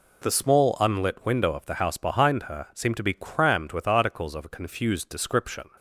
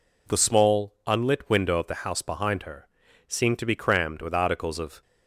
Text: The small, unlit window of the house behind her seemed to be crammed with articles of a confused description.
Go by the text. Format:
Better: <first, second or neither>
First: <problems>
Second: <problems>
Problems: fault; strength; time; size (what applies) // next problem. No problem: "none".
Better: first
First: none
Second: pauses between "her" and "seemed"; at 2.8 s; 0.42 s long // stops before "a confused description"; at 5.0 s